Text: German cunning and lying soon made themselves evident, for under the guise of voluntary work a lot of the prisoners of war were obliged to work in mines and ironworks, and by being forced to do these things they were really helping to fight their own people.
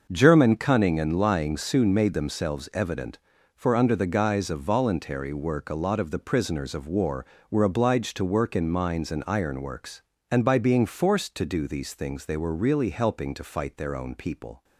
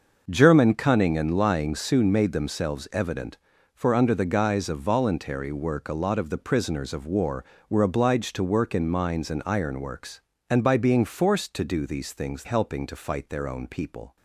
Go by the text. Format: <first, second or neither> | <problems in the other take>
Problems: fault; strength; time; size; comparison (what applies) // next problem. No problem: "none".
first | starts louder than the rest; noticeable; until 1.2 s; 6 dB; noticeable in the first // skips "they were really"; at 12.4 s